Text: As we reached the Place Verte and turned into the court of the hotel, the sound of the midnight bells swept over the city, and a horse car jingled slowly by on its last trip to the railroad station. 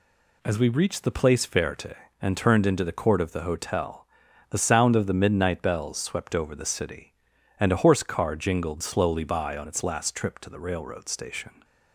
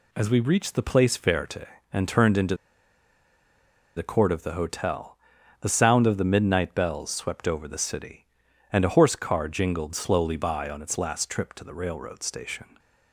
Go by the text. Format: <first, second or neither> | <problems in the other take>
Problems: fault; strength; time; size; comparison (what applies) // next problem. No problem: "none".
first | pauses between "into" and "the"; strong; at 2.5 s; 1.3 s long